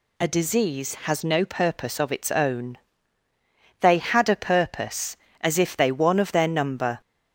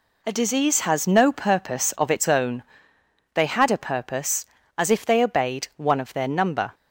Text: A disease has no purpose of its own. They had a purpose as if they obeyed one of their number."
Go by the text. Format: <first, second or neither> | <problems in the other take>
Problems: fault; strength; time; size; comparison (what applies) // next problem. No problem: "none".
second | skips "obeyed"; at 5.9 s